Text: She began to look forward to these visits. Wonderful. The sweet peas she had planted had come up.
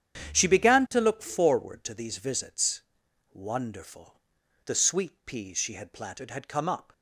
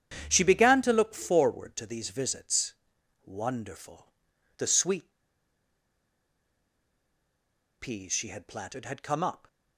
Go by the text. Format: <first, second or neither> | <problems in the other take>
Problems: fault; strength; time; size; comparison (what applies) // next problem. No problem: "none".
first | starts louder than the rest; strong; until 1.2 s; 9 dB; strong in the first // pauses between "sweet" and "peas"; strong; at 5.1 s; 2.6 s long